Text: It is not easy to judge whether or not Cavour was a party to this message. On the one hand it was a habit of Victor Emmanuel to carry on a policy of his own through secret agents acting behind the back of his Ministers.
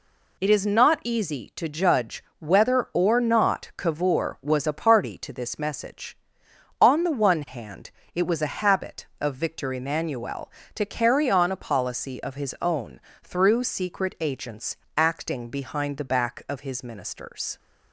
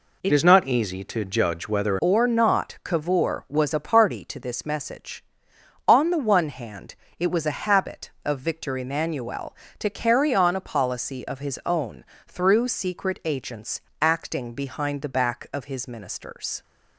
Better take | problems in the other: first | changes voice from "is" to "whether"; from 0.3 to 1.9 s; 1.6 s long // pauses between "hand" and "it"; slight; at 6.9 s; 0.24 s long; slight in the first // pauses between "own" and "through"; slight; at 12.0 s; 0.22 s long; slight in the first // pauses between "agents" and "acting"; slight; at 13.8 s; 0.18 s long; slight in the first

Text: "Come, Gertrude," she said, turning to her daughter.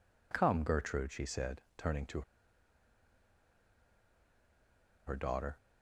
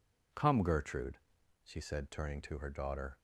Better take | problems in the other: second | pauses between "to" and "her"; strong; at 2.2 s; 2.8 s long

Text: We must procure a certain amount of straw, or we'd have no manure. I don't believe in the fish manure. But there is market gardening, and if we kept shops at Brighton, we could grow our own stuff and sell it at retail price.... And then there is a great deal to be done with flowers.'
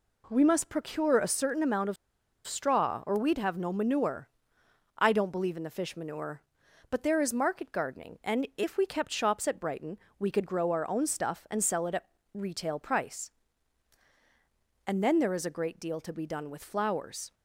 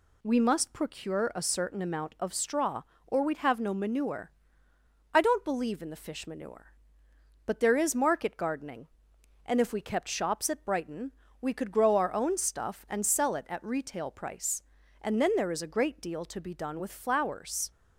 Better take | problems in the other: second | pauses between "of" and "straw"; noticeable; at 1.9 s; 0.51 s long // pauses between "at" and "retail"; slight; at 12.0 s; 0.28 s long

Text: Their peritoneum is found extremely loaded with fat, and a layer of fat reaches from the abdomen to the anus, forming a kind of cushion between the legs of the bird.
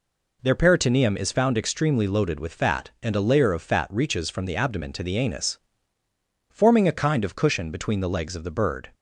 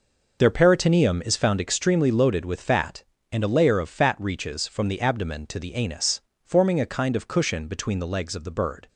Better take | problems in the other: first | starts louder than the rest; noticeable; until 1.7 s; 5.5 dB

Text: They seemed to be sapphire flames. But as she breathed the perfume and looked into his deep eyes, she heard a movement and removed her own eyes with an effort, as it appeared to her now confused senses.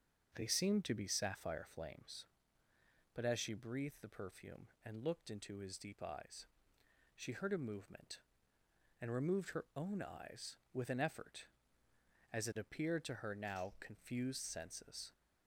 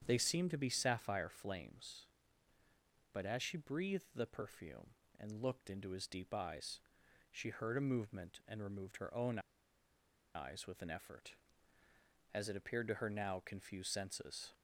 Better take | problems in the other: first | starts louder than the rest; strong; until 1.0 s; 8 dB; also in the first // pauses between "own" and "eyes"; noticeable; at 9.3 s; 0.96 s long

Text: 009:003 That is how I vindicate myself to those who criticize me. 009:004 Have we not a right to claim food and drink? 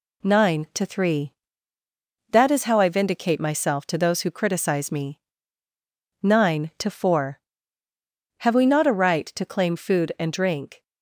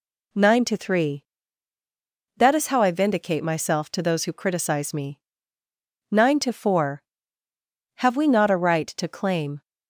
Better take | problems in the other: first | stops before "food and drink"; at 9.6 s

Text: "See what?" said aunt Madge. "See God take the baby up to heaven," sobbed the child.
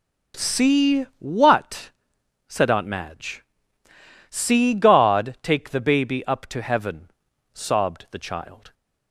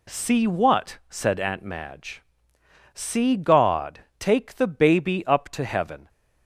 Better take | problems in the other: first | stops before "sobbed the child"; at 6.0 s

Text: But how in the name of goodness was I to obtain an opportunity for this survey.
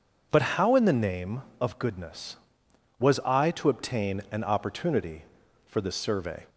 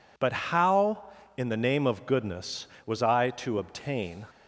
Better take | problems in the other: first | stops before "an opportunity for this survey"; at 4.2 s

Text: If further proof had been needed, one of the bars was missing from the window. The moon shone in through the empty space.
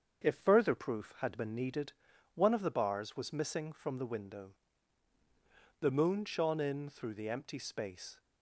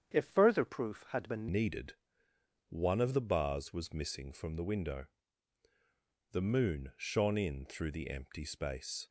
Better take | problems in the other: first | starts louder than the rest; strong; until 1.1 s; 8.5 dB; strong in the first // changes voice at "needed"; from 1.4 s on; 7.6 s long

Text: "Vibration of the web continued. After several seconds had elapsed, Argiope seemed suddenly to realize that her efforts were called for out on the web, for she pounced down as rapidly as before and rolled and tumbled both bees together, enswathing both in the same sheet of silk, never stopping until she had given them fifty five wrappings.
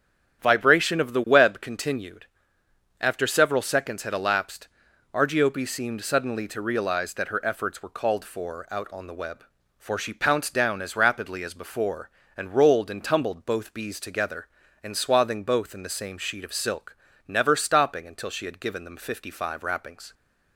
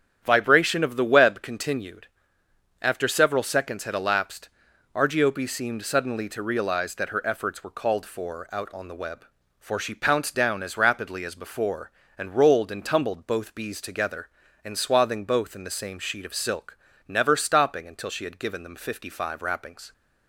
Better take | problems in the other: neither | starts louder than the rest; strong; the same in both

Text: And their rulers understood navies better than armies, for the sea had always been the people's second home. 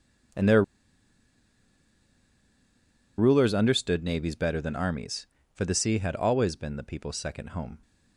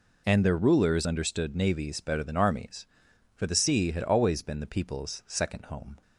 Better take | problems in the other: second | pauses between "their" and "rulers"; strong; at 0.6 s; 2.5 s long

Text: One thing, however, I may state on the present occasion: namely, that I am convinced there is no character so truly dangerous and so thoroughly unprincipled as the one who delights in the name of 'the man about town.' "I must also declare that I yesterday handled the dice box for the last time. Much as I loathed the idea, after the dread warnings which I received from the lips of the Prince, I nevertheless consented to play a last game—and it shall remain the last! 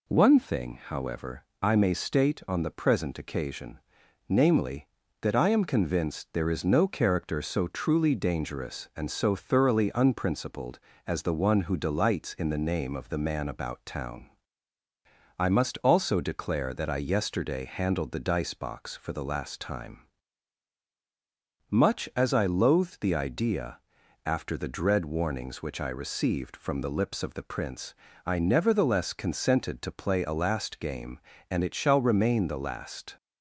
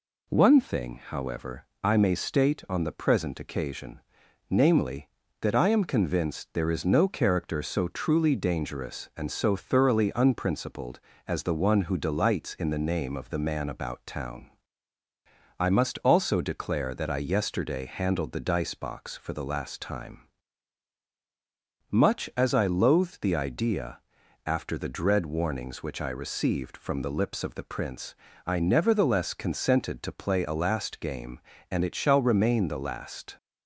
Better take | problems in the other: neither | none

